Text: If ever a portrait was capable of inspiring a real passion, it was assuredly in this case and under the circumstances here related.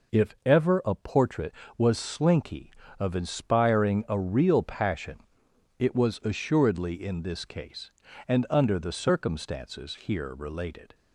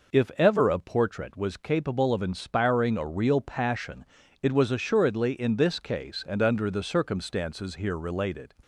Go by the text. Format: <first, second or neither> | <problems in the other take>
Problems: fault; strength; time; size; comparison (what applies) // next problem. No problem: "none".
second | says "slinky" for "capable"; at 1.9 s